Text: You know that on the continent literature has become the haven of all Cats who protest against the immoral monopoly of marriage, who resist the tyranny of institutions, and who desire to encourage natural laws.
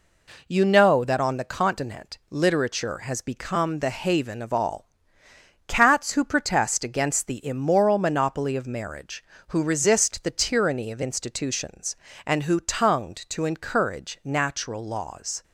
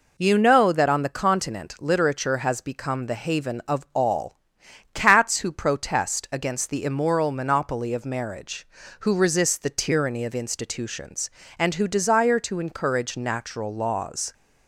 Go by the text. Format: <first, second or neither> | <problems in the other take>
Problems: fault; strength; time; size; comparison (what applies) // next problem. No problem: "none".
second | pauses between "all" and "Cats"; noticeable; at 4.8 s; 0.80 s long; noticeable in the second // says "tongued" for "desire"; at 12.6 s